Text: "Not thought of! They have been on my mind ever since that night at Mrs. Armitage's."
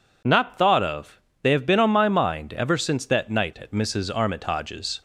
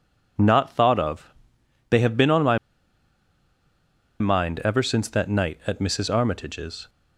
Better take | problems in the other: first | pauses between "my" and "mind"; strong; at 2.5 s; 1.6 s long

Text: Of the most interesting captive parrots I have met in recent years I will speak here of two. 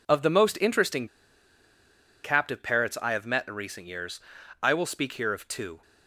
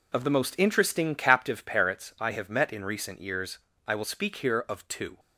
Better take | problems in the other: second | pauses between "interesting" and "captive"; at 1.0 s; 1.1 s long // pauses between "years" and "I"; at 4.2 s; 0.40 s long; slight in the second

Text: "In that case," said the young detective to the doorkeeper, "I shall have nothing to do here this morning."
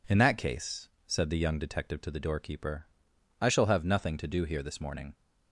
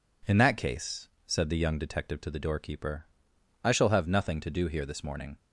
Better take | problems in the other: neither | none

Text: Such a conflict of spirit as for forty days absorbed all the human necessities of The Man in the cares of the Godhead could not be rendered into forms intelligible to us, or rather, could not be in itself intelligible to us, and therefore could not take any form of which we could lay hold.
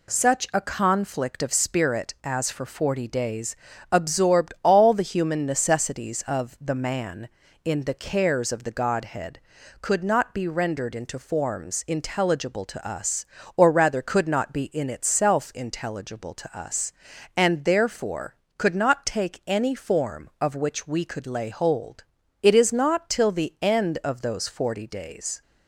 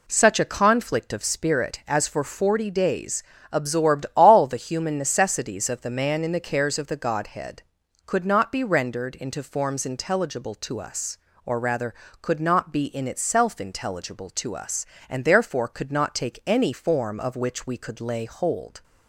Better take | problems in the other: second | pauses between "days" and "absorbed"; slight; at 3.5 s; 0.36 s long; slight in the second // goes on to say "It is not till the end of those forty days"; strong; from 22.4 s on; 3.0 s long

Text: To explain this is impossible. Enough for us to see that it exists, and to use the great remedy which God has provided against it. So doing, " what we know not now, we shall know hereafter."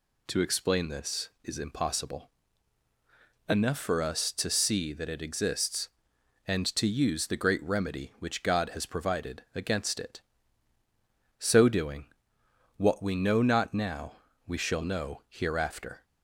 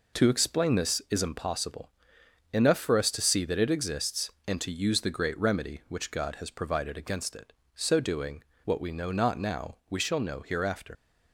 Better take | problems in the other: first | leaves "hereafter" unfinished; at 10.9 s; 80 ms

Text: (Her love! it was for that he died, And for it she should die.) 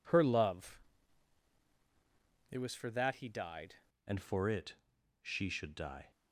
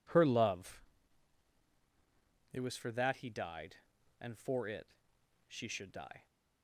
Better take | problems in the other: second | changes voice at "And"; from 4.0 s on; 2.1 s long // pauses between "it" and "she"; noticeable; at 4.7 s; 0.48 s long; noticeable in the second

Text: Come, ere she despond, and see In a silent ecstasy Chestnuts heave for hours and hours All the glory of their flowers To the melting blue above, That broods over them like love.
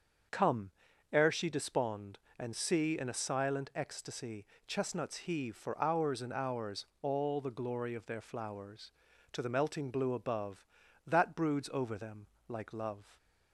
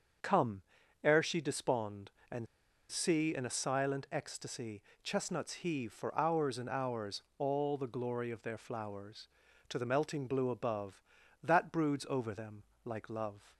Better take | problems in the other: first | starts louder than the rest; until 1.6 s; 6.5 dB; also in the first // pauses between "and" and "see"; at 2.4 s; 0.44 s long // pauses between "ecstasy" and "Chestnuts"; slight; at 4.8 s; 0.22 s long; slight in the first // pauses between "hours" and "All"; slight; at 7.2 s; 0.16 s long; slight in the first // pauses between "them" and "like"; slight; at 12.6 s; 0.22 s long; slight in the first

